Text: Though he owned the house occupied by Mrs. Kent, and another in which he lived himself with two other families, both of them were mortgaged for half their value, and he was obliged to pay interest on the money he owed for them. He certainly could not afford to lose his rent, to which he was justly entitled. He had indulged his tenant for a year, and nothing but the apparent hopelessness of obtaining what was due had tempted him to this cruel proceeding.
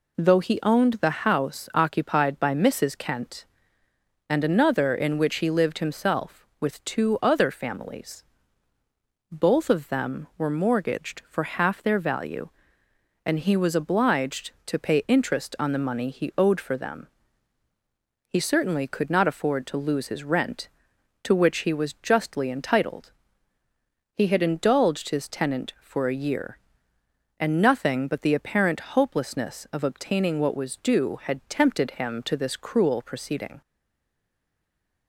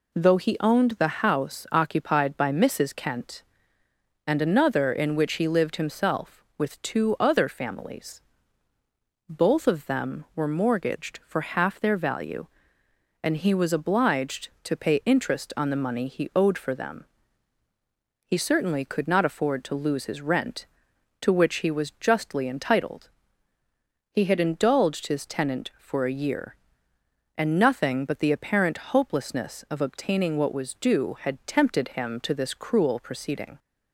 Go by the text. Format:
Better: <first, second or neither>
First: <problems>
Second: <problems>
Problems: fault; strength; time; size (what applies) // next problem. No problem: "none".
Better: second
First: stays silent after the last word; noticeable; from 33.6 s on; 1.4 s long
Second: none